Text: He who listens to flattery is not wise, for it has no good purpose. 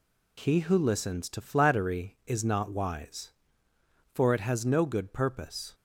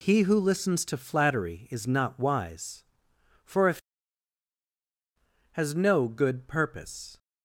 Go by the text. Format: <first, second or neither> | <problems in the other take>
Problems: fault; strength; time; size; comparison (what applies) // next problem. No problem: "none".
first | says "if" for "it"; at 3.6 s